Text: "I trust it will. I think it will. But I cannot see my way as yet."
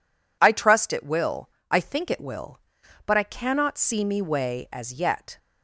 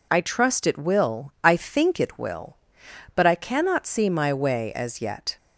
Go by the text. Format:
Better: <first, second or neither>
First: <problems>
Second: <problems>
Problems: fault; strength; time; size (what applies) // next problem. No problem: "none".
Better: second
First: says "me" for "my"; at 4.0 s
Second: none